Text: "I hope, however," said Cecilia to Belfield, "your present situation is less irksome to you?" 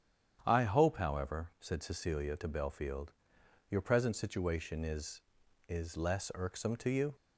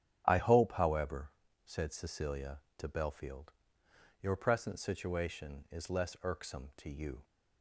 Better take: second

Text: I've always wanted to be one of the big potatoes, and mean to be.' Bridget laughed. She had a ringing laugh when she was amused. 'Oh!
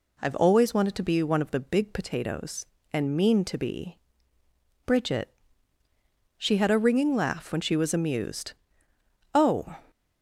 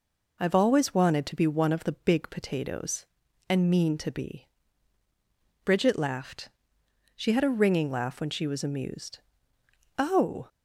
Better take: second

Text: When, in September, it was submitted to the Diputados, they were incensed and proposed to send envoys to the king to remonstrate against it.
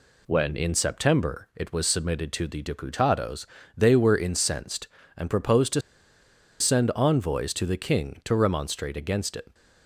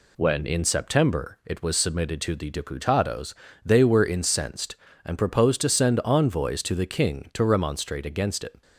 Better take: second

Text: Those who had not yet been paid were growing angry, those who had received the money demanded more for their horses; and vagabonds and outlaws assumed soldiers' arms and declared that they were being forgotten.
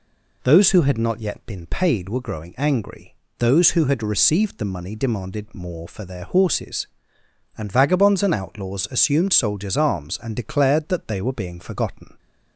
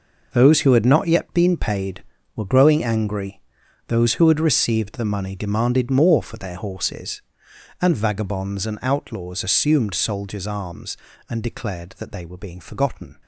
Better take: first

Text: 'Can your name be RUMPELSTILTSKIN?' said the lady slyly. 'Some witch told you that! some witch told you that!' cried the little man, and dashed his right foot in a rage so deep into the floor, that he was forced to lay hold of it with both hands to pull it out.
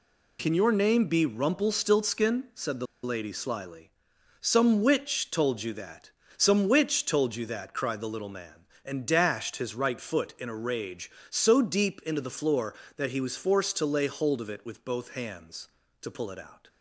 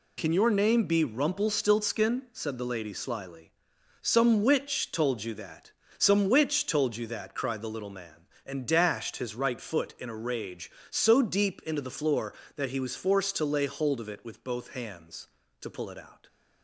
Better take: second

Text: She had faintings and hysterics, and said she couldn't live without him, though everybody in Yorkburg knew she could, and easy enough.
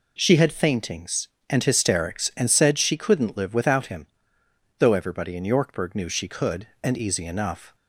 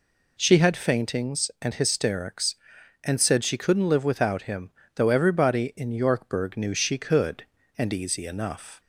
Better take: neither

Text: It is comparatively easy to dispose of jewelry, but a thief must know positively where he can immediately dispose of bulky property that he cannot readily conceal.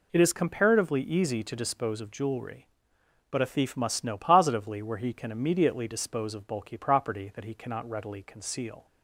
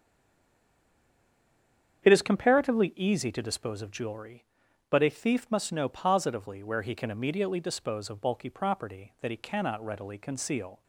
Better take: first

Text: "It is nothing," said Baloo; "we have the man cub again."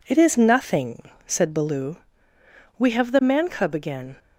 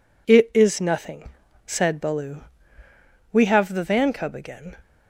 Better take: first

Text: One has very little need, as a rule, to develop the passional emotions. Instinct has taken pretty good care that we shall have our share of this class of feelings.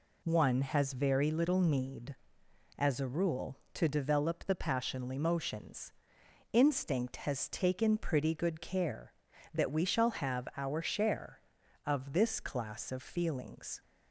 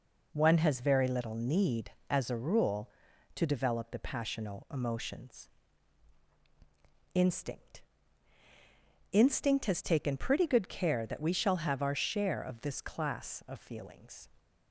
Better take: first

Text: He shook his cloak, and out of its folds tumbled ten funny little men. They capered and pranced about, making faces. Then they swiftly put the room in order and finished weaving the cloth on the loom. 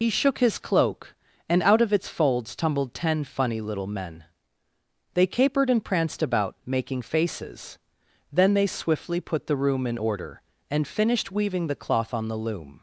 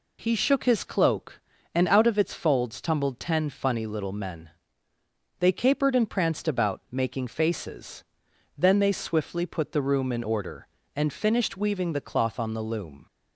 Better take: second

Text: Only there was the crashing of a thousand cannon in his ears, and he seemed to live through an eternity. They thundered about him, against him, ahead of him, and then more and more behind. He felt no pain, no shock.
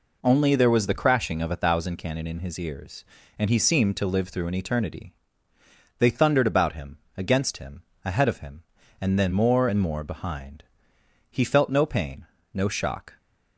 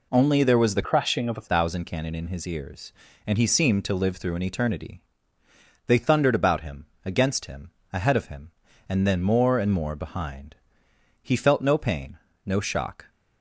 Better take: first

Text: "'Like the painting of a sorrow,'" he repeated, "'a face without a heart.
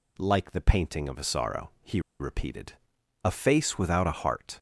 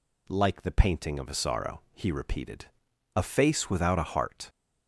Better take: second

